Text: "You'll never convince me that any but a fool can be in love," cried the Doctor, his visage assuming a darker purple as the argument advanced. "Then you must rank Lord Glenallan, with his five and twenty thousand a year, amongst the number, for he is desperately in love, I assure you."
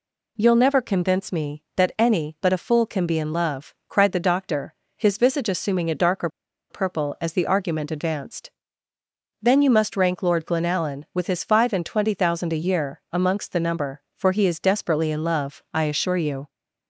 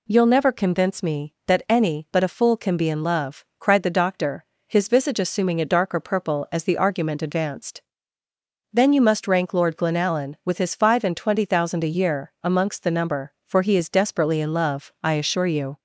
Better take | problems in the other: second | pauses between "darker" and "purple"; at 6.2 s; 0.42 s long

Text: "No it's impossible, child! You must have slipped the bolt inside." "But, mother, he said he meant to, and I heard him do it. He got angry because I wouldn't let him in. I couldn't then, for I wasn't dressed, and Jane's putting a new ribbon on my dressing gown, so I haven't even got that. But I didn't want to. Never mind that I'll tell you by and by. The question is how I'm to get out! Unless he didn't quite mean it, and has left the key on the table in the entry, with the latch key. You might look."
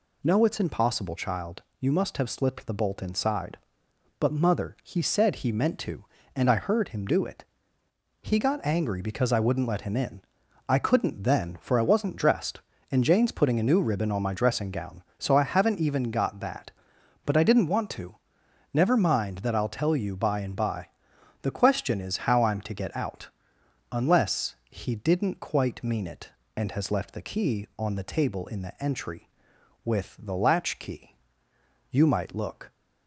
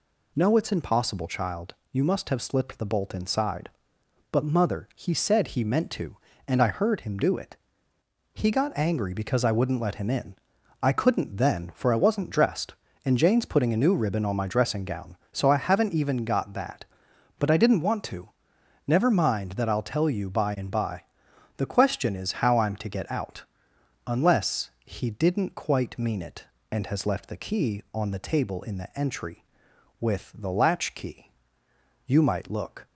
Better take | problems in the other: neither | none

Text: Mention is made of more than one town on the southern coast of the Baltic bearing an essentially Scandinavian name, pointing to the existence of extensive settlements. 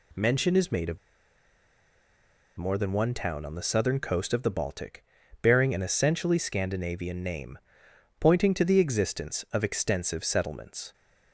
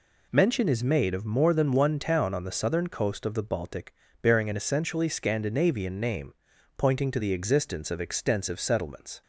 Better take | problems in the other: second | pauses between "of" and "more"; strong; at 0.9 s; 1.6 s long // pauses between "Baltic" and "bearing"; slight; at 5.0 s; 0.36 s long; slight in the second

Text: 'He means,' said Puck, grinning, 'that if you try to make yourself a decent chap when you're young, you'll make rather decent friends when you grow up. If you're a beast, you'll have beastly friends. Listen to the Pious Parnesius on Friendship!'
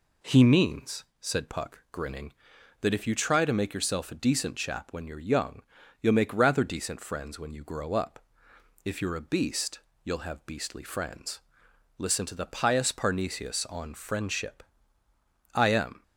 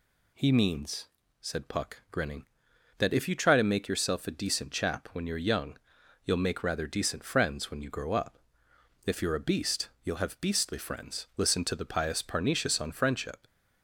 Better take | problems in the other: second | goes on to say "I am"; slight; from 15.5 s on; 0.48 s long

